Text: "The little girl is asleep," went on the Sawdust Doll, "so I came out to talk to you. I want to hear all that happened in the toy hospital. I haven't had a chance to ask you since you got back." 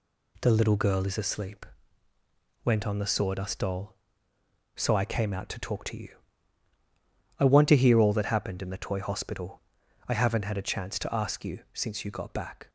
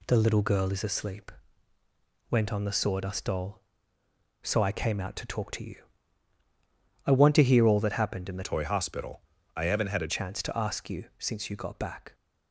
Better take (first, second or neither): first